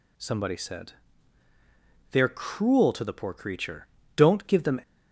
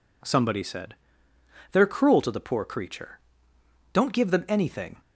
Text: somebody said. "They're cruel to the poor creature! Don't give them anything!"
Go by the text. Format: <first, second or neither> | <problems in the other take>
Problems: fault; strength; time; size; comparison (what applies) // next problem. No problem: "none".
second | stops before "anything"; at 4.8 s